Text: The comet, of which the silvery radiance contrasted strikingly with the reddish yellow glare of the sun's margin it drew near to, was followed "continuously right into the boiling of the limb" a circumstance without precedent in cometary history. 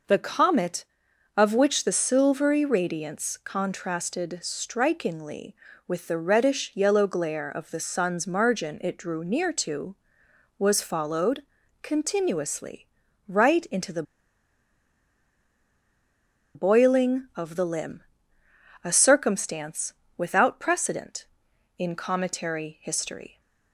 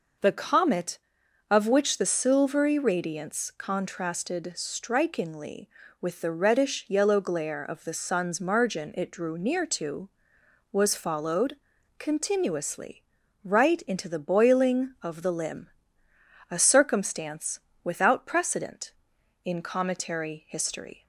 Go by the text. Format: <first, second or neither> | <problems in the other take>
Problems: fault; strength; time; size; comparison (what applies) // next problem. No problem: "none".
second | pauses between "followed" and "continuously"; at 11.4 s; 0.38 s long; also in the second // pauses between "continuously" and "right"; at 12.8 s; 0.40 s long; also in the second // pauses between "the" and "boiling"; strong; at 14.0 s; 2.5 s long // pauses between "limb" and "a"; noticeable; at 18.0 s; 0.80 s long; noticeable in the second // pauses between "circumstance" and "without"; slight; at 19.9 s; 0.24 s long; slight in the second